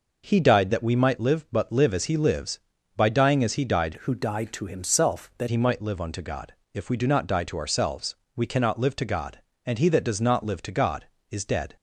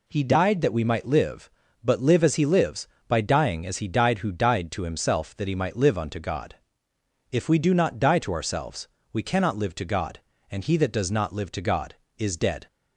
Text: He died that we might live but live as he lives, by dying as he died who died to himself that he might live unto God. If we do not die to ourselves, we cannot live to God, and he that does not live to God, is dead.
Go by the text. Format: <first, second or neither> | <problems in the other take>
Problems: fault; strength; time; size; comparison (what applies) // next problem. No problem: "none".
second | changes voice from "who" to "that"; from 4.0 to 5.4 s; 1.4 s long